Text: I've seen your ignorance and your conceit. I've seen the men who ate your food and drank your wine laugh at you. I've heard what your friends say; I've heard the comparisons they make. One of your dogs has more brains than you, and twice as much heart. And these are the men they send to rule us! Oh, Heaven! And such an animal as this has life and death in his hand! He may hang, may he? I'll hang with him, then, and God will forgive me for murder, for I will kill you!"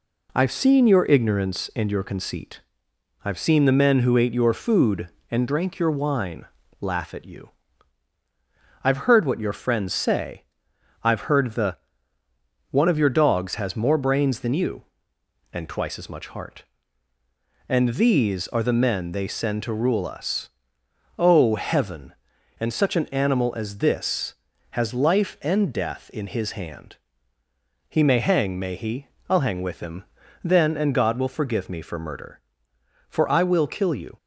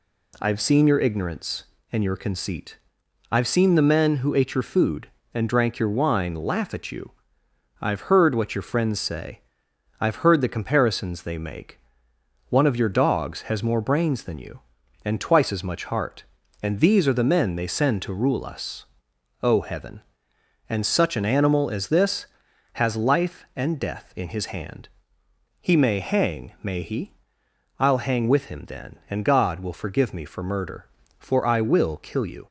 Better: second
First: pauses between "wine" and "laugh"; slight; at 6.4 s; 0.34 s long // skips "comparisons they make"; at 12.2 s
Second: none

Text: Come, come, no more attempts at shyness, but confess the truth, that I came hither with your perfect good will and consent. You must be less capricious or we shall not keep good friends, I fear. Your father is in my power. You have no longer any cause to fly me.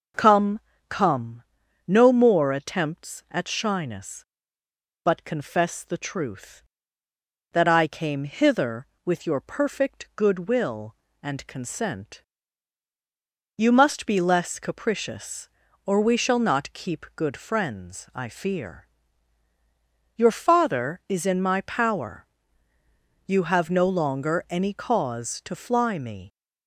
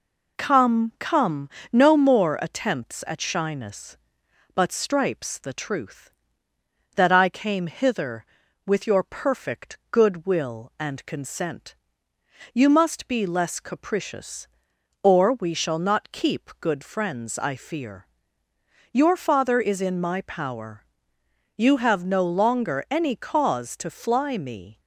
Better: first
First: none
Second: says "stripes" for "confess"; at 4.7 s

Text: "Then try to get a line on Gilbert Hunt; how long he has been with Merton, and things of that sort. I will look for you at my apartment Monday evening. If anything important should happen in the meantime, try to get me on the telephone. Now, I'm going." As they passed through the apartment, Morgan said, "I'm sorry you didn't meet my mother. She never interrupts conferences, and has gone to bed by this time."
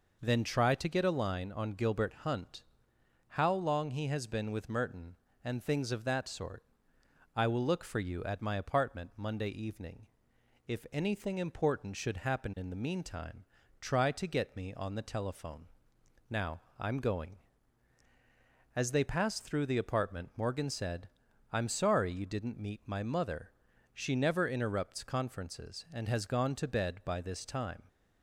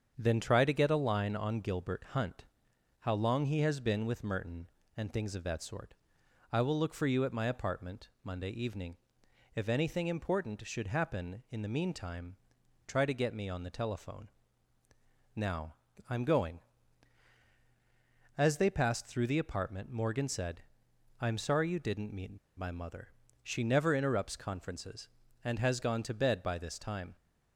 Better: first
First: none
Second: starts louder than the rest; strong; until 1.1 s; 7.5 dB // pauses between "apartment" and "Monday"; slight; at 8.0 s; 0.16 s long // pauses between "meet" and "my"; slight; at 22.3 s; 0.19 s long

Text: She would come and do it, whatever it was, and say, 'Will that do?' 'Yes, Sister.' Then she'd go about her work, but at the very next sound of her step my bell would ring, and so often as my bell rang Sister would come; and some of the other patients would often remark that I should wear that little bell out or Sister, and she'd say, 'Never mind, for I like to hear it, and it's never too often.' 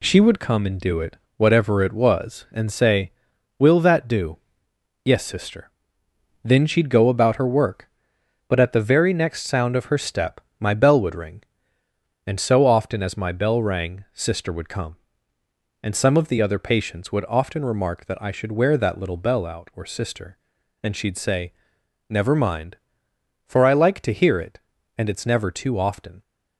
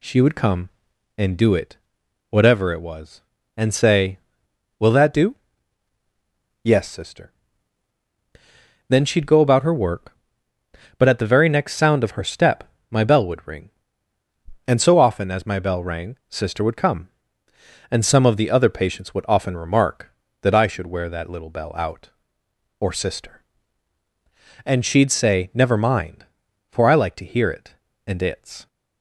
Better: first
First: pauses between "step" and "my"; slight; at 10.4 s; 0.18 s long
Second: pauses between "step" and "my"; slight; at 12.6 s; 0.26 s long // stops before "never too often"; at 28.6 s

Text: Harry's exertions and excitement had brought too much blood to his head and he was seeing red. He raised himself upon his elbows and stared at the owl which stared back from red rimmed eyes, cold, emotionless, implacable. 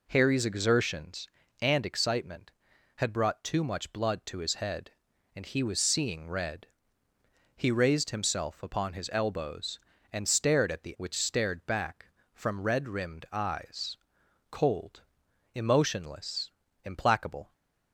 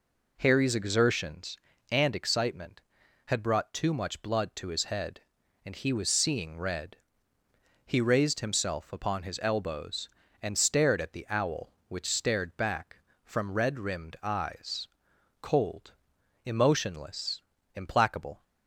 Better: second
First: skips "owl"; at 10.9 s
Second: none

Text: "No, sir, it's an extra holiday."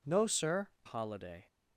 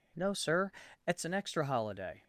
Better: second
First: skips "it's an extra"; at 0.7 s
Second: none

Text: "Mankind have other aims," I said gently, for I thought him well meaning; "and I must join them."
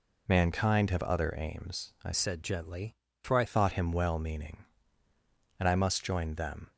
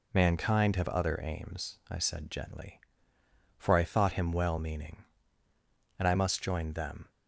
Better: second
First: changes voice from "said" to "I"; from 2.1 to 3.4 s; 1.3 s long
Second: none

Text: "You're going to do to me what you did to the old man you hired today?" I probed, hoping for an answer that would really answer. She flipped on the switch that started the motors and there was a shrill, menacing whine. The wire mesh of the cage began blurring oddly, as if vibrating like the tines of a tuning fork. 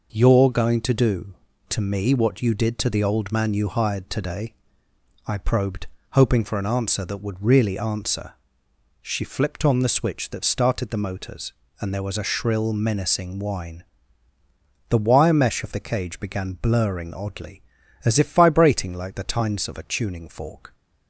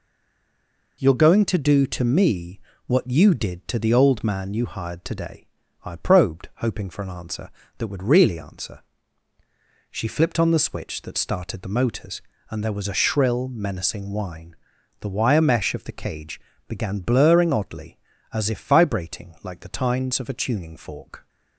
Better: first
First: none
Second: stays silent before the first word; until 0.9 s; 0.9 s long // pauses between "me" and "what"; slight; at 2.5 s; 0.28 s long // pauses between "cage" and "began"; slight; at 16.3 s; 0.26 s long

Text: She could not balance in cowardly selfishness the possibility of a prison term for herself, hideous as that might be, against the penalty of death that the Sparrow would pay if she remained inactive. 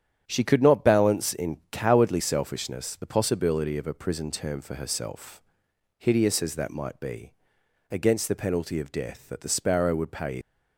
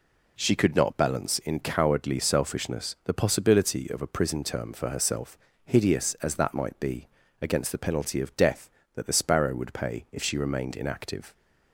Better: second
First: starts louder than the rest; strong; until 1.2 s; 9 dB // stops before "if she remained inactive"; at 10.4 s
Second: none

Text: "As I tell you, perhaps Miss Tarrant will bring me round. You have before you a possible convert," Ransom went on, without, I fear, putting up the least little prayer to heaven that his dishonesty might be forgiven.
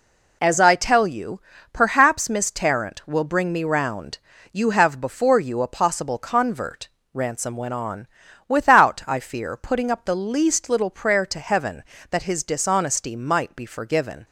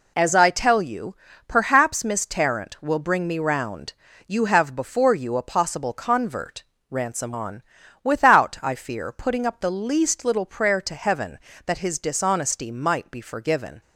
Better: first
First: none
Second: skips "went"; at 7.3 s

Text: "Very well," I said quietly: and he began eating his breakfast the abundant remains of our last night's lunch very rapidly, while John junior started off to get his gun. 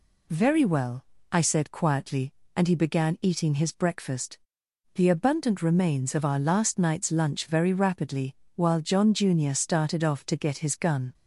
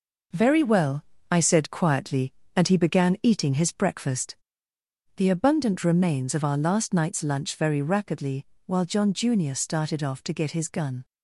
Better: first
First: pauses between "breakfast" and "the"; noticeable; at 4.3 s; 0.58 s long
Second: gets quieter; noticeable; throughout; 5.5 dB // pauses between "breakfast" and "the"; noticeable; at 4.3 s; 0.80 s long

